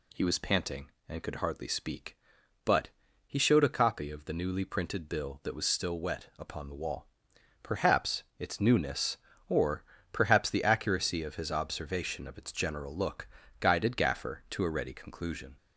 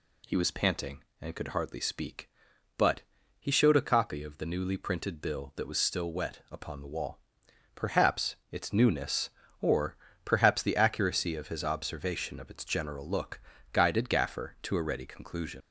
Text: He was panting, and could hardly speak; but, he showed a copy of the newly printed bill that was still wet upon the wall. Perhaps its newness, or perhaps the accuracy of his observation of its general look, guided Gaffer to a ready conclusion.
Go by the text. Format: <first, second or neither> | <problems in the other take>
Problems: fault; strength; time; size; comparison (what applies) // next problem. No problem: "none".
first | pauses between "or" and "perhaps"; slight; at 9.9 s; 0.30 s long; slight in the first // leaves "conclusion" unfinished; at 15.6 s; 85 ms